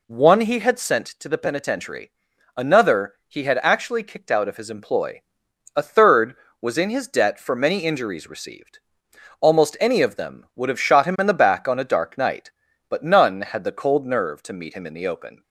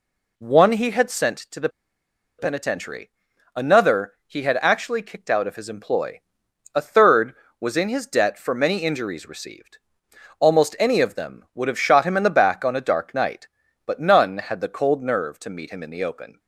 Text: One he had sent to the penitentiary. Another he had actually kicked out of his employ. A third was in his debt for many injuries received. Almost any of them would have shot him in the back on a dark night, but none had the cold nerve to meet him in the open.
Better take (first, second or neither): first